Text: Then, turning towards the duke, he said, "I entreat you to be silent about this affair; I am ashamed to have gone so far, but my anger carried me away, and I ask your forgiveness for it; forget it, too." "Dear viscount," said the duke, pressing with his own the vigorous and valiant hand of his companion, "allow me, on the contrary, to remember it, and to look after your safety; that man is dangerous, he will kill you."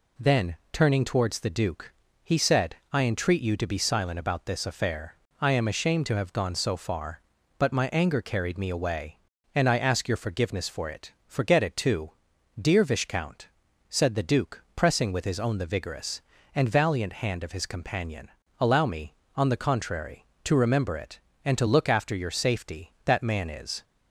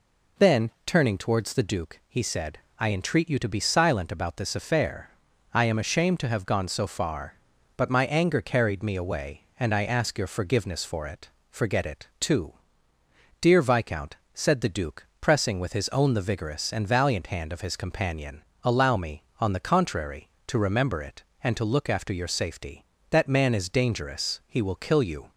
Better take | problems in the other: second | stops before "dangerous he will kill you"; at 23.8 s

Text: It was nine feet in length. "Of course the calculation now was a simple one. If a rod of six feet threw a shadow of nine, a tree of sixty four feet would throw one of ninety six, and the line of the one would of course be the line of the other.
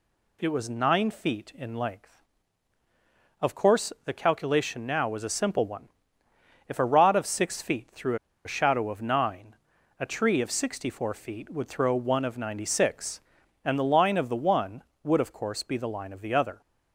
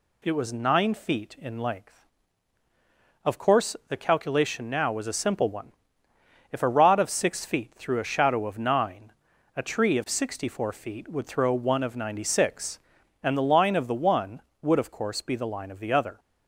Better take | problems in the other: second | pauses between "threw" and "a"; slight; at 8.1 s; 0.29 s long

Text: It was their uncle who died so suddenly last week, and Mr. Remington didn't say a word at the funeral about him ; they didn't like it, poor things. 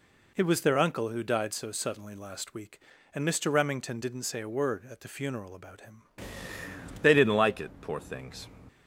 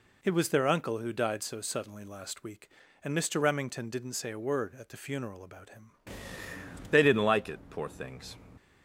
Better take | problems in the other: neither | none

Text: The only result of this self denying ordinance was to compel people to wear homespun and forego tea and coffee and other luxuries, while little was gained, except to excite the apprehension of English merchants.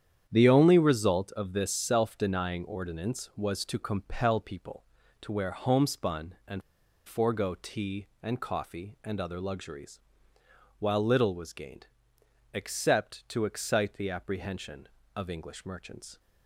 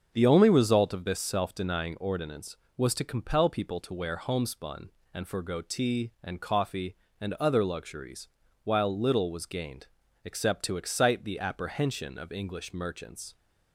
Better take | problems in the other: second | starts louder than the rest; strong; until 1.2 s; 9 dB; also in the second // pauses between "and" and "forego"; at 6.6 s; 0.45 s long

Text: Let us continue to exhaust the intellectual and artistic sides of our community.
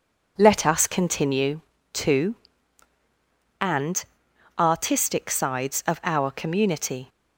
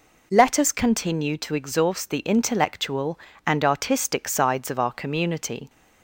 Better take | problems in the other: second | skips "exhaust the intellectual"; at 2.9 s // pauses between "and" and "artistic"; noticeable; at 4.0 s; 0.54 s long

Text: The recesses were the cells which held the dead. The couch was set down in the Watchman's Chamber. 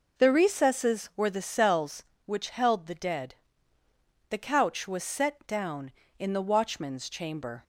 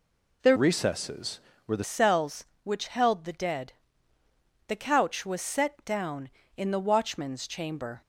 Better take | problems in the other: first | changes voice from "recesses" to "the"; from 0.5 to 1.8 s; 1.3 s long

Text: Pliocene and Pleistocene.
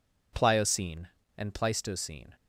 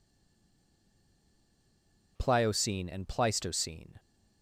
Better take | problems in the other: first | stays silent before the first word; until 2.1 s; 2.1 s long

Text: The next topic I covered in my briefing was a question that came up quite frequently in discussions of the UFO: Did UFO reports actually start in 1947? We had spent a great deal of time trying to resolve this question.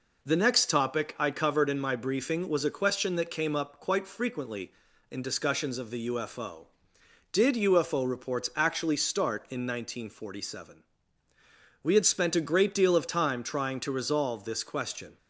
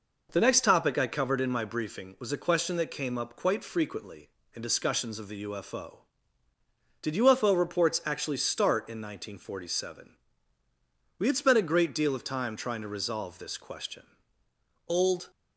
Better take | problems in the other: first | goes on to say "Old"; slight; from 14.8 s on; 0.42 s long

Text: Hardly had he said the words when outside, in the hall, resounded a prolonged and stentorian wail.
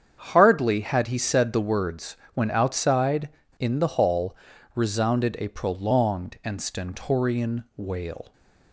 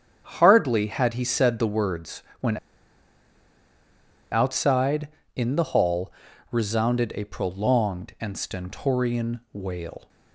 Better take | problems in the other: first | starts louder than the rest; strong; until 1.2 s; 7.5 dB; strong in the first // pauses between "words" and "when"; slight; at 2.2 s; 0.16 s long; slight in the first // pauses between "when" and "outside"; strong; at 2.5 s; 1.7 s long

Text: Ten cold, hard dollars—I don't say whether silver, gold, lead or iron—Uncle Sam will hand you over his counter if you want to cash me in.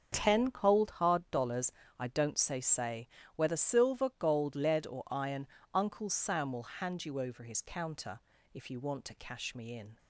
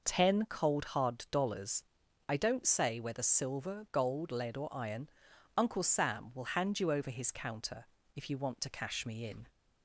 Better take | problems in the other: second | starts louder than the rest; until 1.1 s; 6.5 dB // says "say" twice; at 2.5 s // pauses between "counter" and "if"; slight; at 8.1 s; 0.34 s long; slight in the second

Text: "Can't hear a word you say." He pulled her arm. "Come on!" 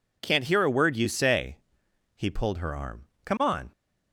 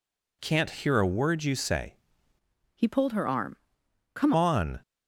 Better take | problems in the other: first | changes voice from "He" to "Come"; from 2.7 to 4.3 s; 1.6 s long

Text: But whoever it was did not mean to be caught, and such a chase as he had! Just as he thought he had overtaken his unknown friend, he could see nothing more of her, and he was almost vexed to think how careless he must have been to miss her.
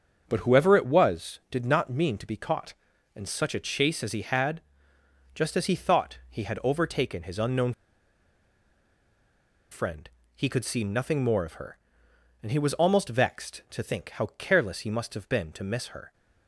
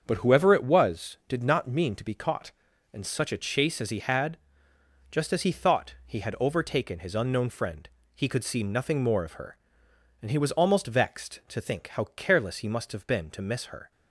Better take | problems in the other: second | starts louder than the rest; until 1.2 s; 7 dB; also in the second // pauses between "unknown" and "friend"; strong; at 7.7 s; 1.9 s long

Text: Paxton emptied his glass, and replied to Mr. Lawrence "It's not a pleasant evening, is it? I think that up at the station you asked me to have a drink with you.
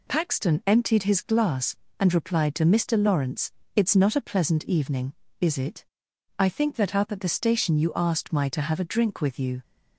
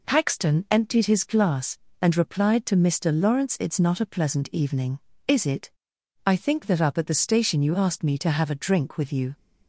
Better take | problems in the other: second | pauses between "Lawrence" and "It's"; slight; at 3.5 s; 0.24 s long // says "my" for "me"; at 8.3 s

